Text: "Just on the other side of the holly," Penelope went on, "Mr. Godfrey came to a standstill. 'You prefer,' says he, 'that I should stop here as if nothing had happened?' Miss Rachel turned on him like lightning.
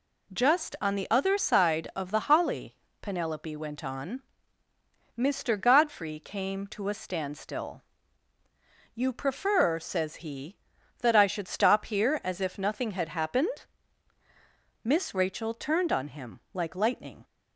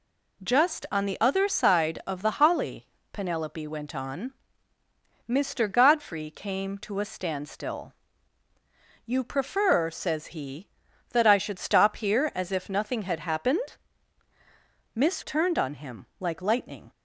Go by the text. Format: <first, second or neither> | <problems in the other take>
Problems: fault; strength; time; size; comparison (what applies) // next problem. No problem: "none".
first | skips "Rachel"; at 15.2 s